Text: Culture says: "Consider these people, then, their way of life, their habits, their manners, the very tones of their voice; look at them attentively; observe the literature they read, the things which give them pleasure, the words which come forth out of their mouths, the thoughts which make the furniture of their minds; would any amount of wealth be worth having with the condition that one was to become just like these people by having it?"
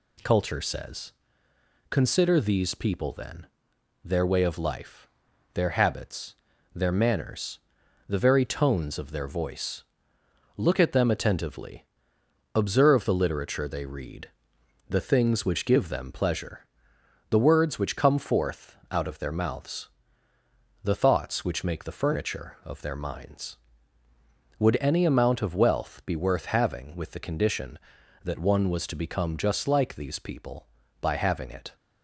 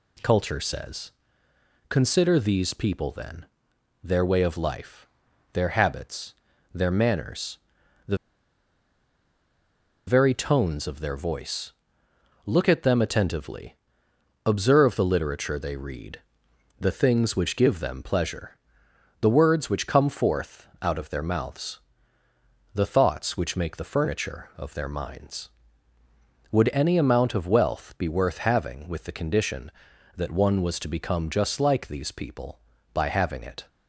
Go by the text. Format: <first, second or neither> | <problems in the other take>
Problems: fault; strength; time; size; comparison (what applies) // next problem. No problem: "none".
first | pauses between "the" and "very"; strong; at 8.1 s; 1.9 s long // pauses between "forth" and "out"; slight; at 20.6 s; 0.16 s long; slight in the first